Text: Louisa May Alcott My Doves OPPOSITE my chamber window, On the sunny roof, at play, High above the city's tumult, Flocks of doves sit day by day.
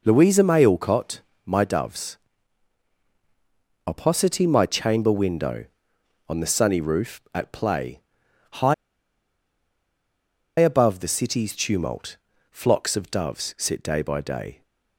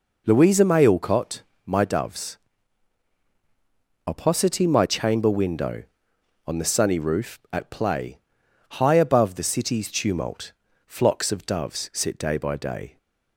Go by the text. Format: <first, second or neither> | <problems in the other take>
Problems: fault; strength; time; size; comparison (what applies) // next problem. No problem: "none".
second | pauses between "Alcott" and "My"; slight; at 1.1 s; 0.26 s long; slight in the second // pauses between "Doves" and "OPPOSITE"; strong; at 2.1 s; 1.6 s long; strong in the second // pauses between "High" and "above"; strong; at 8.7 s; 1.8 s long